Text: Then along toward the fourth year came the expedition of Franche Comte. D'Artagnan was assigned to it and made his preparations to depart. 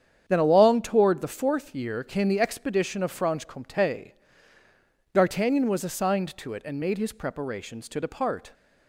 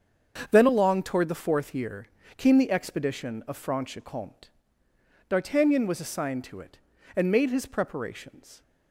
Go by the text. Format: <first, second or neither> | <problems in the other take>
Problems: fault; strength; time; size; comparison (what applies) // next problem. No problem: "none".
first | starts louder than the rest; until 1.5 s; 7 dB; strong in the first // pauses between "year" and "came"; slight; at 2.0 s; 0.32 s long // stops before "to depart"; at 8.6 s